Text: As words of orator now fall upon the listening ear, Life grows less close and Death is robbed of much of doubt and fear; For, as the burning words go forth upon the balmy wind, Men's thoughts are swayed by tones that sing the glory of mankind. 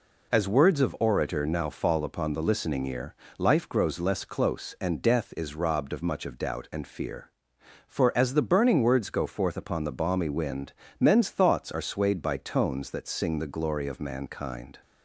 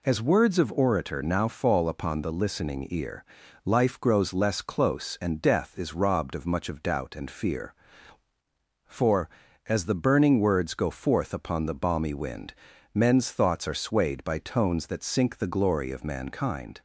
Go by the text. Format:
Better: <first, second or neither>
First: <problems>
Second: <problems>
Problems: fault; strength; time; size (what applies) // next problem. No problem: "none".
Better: first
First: none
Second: says "sink" for "sing"; at 15.0 s